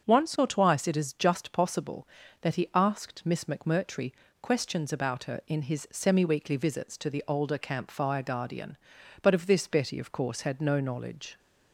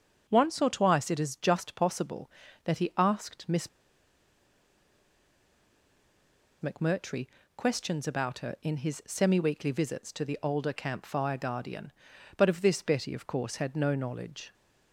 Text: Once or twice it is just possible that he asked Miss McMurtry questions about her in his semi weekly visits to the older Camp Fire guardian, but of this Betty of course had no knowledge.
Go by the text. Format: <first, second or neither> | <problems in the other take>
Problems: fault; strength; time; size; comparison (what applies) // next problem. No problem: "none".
first | starts louder than the rest; until 1.3 s; 6.5 dB; also in the first // pauses between "Miss" and "McMurtry"; strong; at 3.6 s; 2.9 s long // pauses between "McMurtry" and "questions"; slight; at 7.2 s; 0.30 s long; slight in the first